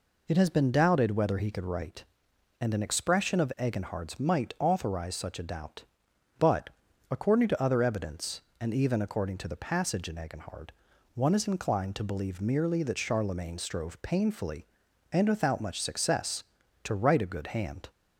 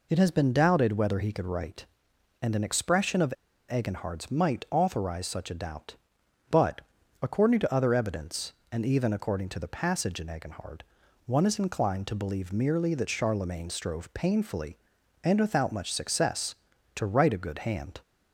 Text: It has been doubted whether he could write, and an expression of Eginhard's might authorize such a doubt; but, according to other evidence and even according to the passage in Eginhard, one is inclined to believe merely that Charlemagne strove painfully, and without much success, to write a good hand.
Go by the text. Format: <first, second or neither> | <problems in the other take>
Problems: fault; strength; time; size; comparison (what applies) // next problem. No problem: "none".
first | pauses between "of" and "Eginhard's"; at 3.3 s; 0.39 s long